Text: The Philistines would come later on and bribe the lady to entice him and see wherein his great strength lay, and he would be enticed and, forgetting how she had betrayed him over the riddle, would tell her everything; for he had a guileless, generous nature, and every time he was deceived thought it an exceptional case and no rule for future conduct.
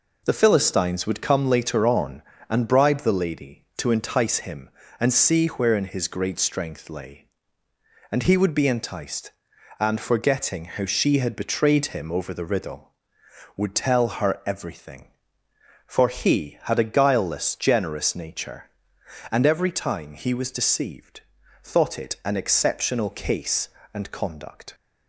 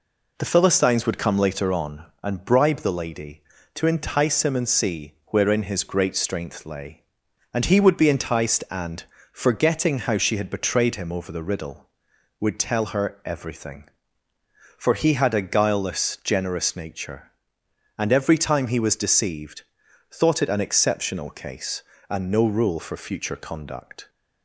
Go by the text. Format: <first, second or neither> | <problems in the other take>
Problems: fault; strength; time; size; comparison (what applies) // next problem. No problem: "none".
second | pauses between "deceived" and "thought"; at 21.2 s; 0.42 s long; noticeable in the second // skips "no rule for future"; at 24.1 s